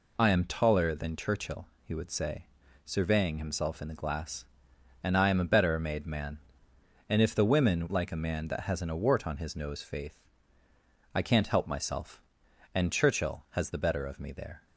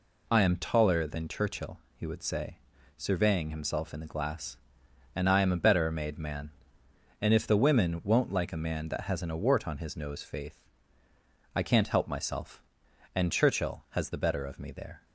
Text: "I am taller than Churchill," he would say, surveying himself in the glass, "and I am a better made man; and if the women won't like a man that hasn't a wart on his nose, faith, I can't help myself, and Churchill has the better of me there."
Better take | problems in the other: second | skips "won't"; at 7.9 s

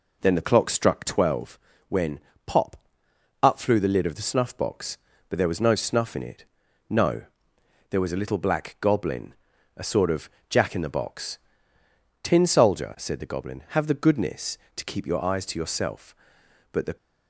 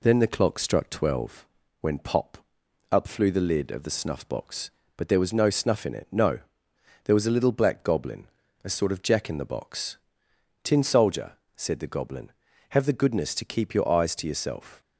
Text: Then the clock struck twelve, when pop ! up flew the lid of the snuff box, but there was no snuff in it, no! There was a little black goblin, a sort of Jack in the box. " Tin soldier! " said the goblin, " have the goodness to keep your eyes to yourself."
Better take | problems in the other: second | pauses between "when" and "pop"; slight; at 2.1 s; 0.28 s long // pauses between "of" and "Jack"; slight; at 10.2 s; 0.20 s long // goes on to say "But the"; slight; from 16.7 s on; 0.24 s long

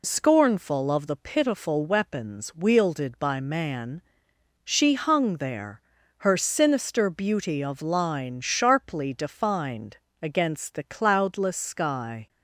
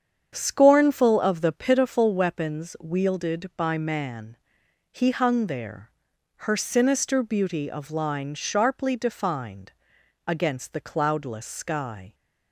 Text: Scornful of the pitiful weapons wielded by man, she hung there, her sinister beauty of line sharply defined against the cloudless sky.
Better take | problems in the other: first | starts louder than the rest; strong; until 1.3 s; 8 dB // says "he" for "she"; at 4.8 s // pauses between "defined" and "against"; noticeable; at 9.6 s; 0.56 s long; slight in the first

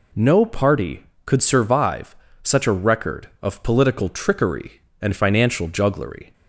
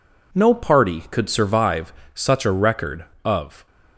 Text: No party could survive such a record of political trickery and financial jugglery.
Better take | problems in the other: first | pauses between "survive" and "such"; slight; at 1.9 s; 0.22 s long; slight in the first // stops before "political trickery and financial jugglery"; at 3.6 s

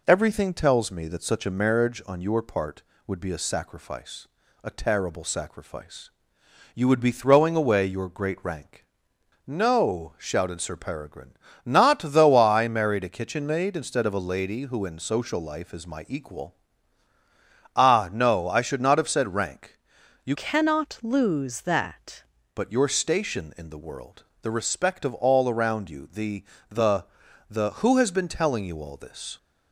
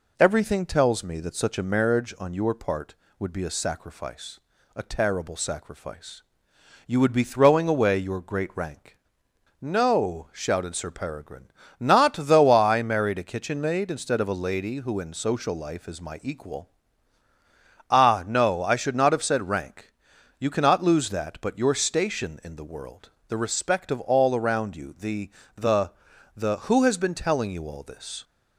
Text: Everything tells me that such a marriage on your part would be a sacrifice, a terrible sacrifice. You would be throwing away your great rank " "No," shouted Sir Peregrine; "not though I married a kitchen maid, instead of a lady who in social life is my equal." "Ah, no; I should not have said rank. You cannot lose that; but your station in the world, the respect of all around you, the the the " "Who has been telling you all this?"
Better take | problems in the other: second | changes voice from "cannot" to "that"; from 20.3 to 22.2 s; 1.9 s long // pauses between "the" and "the"; slight; at 26.4 s; 0.24 s long; slight in the second // pauses between "the" and "the"; at 27.0 s; 0.44 s long; also in the second

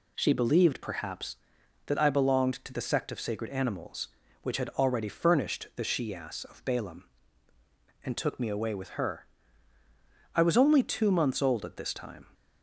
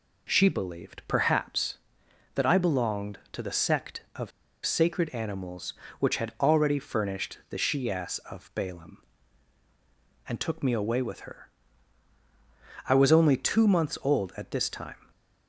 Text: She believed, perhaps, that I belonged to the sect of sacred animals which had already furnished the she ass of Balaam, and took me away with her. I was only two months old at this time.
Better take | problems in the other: first | pauses between "of" and "sacred"; slight; at 4.3 s; 0.35 s long

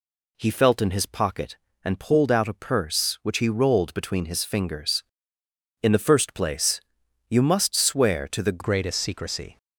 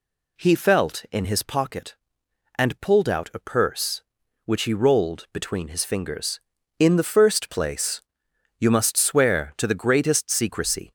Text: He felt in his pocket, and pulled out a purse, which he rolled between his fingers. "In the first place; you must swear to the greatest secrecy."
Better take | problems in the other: second | changes voice at "greatest"; from 8.6 s on; 0.9 s long

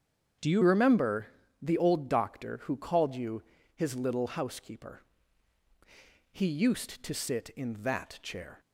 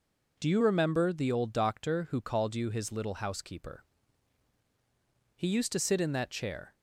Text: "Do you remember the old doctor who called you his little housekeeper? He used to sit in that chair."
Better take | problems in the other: second | starts louder than the rest; strong; until 1.7 s; 8 dB // changes voice at "remember"; from 0.6 s on; 7.9 s long // pauses between "remember" and "the"; slight; at 1.2 s; 0.34 s long // pauses between "you" and "his"; slight; at 3.4 s; 0.32 s long

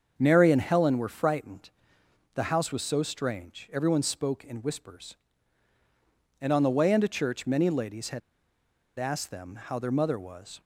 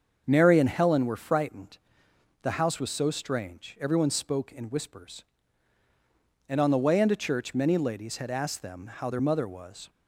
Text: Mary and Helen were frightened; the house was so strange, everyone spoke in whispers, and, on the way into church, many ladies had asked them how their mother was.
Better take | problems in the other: second | starts louder than the rest; until 1.1 s; 7 dB; also in the second // pauses between "had" and "asked"; noticeable; at 8.2 s; 0.78 s long

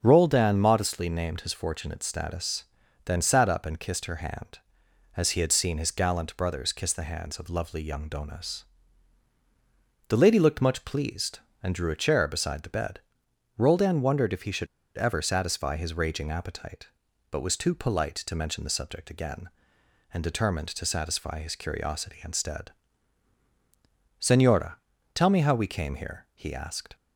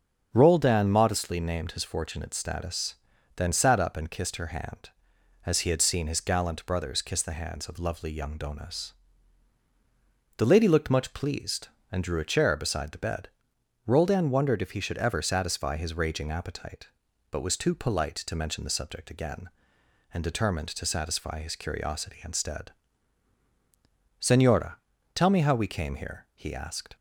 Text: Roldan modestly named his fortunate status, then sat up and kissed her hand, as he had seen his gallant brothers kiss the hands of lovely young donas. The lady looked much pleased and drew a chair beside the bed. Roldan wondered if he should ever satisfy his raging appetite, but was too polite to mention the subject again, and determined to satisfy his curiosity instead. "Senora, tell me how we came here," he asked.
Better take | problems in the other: second | starts louder than the rest; until 1.0 s; 7 dB; also in the second // pauses between "should" and "ever"; slight; at 14.6 s; 0.30 s long

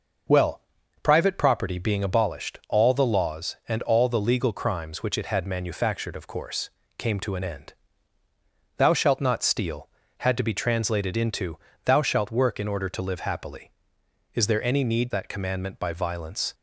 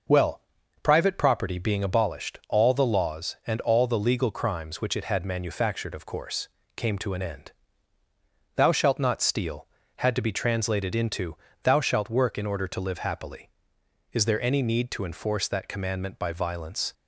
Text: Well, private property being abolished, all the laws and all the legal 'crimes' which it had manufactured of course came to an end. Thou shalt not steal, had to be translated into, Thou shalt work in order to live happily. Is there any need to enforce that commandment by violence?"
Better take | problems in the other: second | pauses between "course" and "came"; slight; at 6.6 s; 0.28 s long; slight in the second // skips "to enforce"; at 15.1 s

